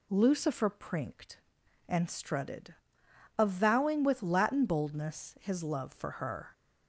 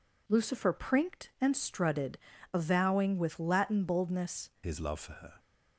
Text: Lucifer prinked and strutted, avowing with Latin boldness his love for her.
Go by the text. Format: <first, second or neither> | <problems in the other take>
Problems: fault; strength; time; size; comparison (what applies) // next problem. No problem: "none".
first | changes voice at "his"; from 4.6 s on; 0.7 s long